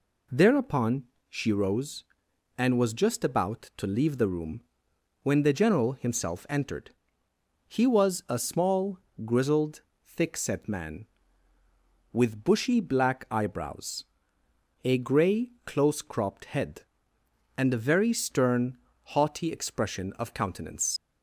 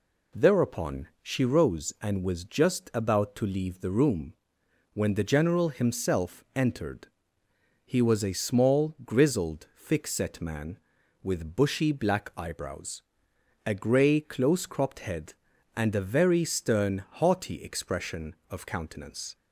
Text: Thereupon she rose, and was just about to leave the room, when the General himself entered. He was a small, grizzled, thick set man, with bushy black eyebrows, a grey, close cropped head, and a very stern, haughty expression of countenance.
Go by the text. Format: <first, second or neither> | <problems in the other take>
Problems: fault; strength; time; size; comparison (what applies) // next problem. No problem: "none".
second | pauses between "Thereupon" and "she"; slight; at 1.0 s; 0.26 s long // leaves "countenance" unfinished; at 20.9 s; 70 ms